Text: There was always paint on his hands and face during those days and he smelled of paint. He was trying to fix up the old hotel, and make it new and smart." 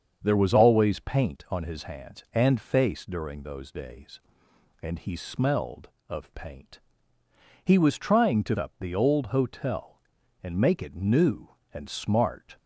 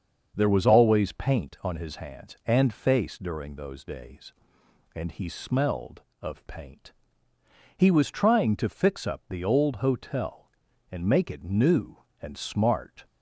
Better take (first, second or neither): second